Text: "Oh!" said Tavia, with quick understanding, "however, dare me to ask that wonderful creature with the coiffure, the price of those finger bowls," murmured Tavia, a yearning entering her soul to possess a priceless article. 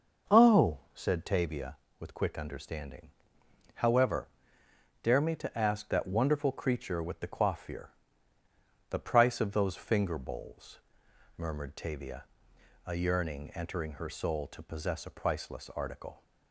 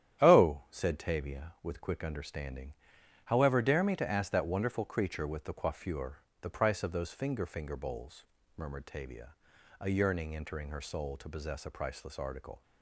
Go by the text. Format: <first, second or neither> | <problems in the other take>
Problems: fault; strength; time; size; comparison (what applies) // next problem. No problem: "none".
first | starts louder than the rest; strong; until 1.3 s; 10.5 dB // says "finger" twice; at 7.4 s